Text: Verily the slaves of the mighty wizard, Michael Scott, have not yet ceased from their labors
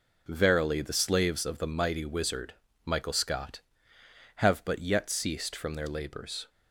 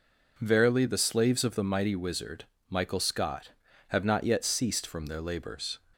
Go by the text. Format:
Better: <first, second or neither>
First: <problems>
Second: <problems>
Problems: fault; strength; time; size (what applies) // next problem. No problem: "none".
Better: second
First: says "but" for "not"; at 4.6 s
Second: none